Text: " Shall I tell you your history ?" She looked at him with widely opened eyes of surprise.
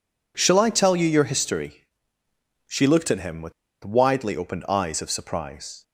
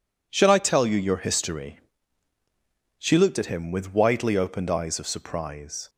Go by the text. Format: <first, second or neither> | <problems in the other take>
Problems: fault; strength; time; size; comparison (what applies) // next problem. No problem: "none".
second | pauses between "with" and "widely"; slight; at 3.5 s; 0.32 s long